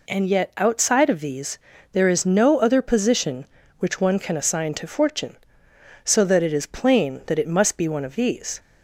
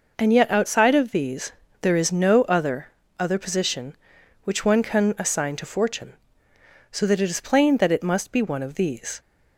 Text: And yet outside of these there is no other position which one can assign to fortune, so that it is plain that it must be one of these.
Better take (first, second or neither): first